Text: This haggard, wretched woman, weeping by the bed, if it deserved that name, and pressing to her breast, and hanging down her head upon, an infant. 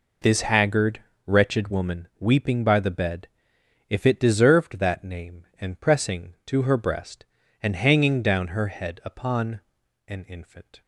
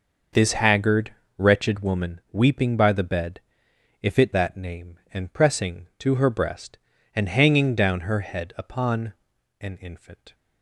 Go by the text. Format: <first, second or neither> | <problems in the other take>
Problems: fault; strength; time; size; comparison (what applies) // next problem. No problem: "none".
first | skips "deserved"; at 4.3 s